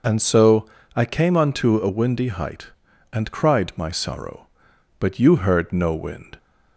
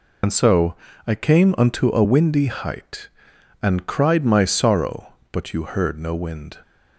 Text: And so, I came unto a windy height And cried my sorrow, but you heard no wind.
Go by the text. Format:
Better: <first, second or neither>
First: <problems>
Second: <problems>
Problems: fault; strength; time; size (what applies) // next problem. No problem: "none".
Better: first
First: none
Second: loses the start of "And"; at 0.2 s; 45 ms